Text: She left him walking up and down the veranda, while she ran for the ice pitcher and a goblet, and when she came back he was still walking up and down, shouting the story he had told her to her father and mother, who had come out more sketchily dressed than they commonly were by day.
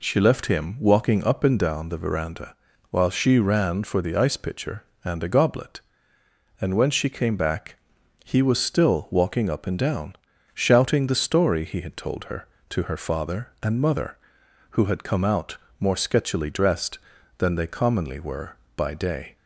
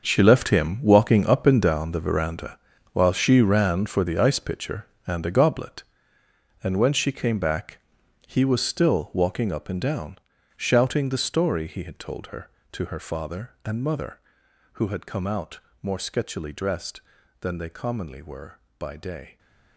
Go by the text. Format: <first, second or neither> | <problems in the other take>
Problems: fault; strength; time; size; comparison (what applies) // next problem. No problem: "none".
first | gets quieter; strong; throughout; 13.5 dB // pauses between "back" and "he"; noticeable; at 7.7 s; 0.48 s long; noticeable in the first // pauses between "out" and "more"; slight; at 15.5 s; 0.22 s long; slight in the first